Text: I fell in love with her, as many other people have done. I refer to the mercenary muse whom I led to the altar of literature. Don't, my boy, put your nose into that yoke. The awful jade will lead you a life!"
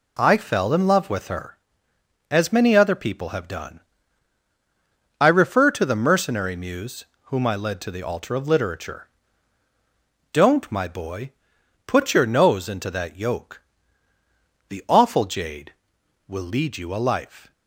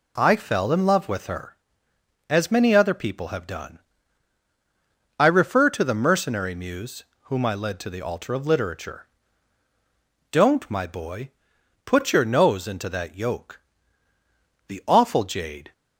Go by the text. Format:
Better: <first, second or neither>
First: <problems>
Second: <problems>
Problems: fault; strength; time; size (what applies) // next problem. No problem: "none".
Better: first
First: pauses between "muse" and "whom"; slight; at 7.0 s; 0.20 s long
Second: pauses between "muse" and "whom"; slight; at 7.0 s; 0.20 s long // stops before "will lead you a life"; at 15.7 s